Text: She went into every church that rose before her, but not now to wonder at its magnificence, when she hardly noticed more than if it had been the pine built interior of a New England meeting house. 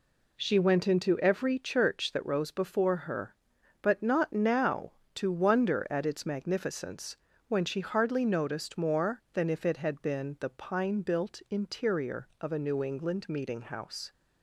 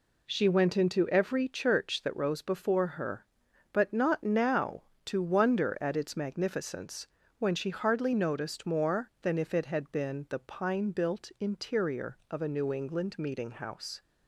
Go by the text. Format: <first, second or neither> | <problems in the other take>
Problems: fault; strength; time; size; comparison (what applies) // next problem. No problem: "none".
neither | none